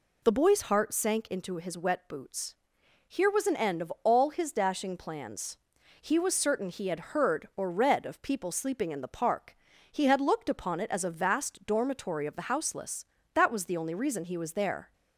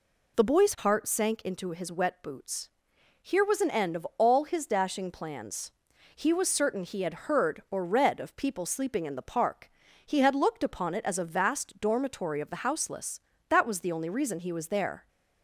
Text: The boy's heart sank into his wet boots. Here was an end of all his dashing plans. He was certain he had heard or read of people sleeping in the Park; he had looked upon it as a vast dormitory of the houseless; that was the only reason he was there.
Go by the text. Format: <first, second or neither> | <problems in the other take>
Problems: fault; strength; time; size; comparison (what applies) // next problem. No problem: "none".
neither | none